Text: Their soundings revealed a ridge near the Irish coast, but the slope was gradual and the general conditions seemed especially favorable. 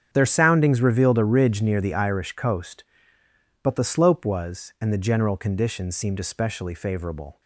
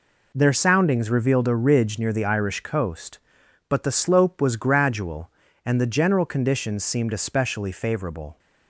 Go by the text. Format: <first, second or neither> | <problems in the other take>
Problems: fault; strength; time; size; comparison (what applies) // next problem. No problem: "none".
second | starts louder than the rest; strong; until 1.1 s; 8 dB // skips "gradual"; at 4.7 s